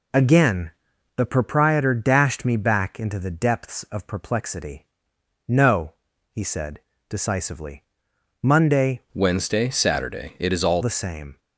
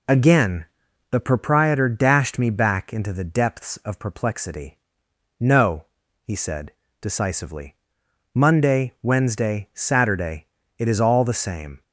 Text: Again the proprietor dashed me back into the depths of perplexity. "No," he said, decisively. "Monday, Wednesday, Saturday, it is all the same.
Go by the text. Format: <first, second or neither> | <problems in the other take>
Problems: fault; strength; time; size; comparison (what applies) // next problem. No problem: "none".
second | pauses between "Again" and "the"; noticeable; at 0.7 s; 0.46 s long; noticeable in the second // changes voice from "Wednesday" to "all"; from 9.1 to 10.8 s; 1.7 s long